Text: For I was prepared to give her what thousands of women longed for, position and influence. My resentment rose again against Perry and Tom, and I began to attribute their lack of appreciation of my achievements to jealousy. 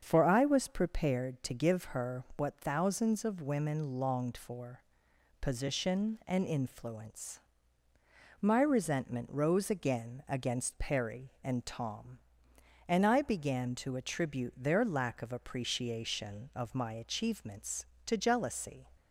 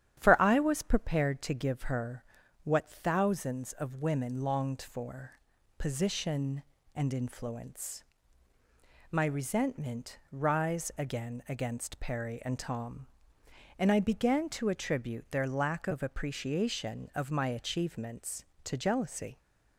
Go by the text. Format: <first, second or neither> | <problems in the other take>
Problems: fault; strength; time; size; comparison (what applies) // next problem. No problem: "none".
first | starts louder than the rest; strong; until 1.2 s; 10 dB; strong in the first // pauses between "her" and "what"; at 2.2 s; 0.40 s long // says "rise" for "rose"; at 10.3 s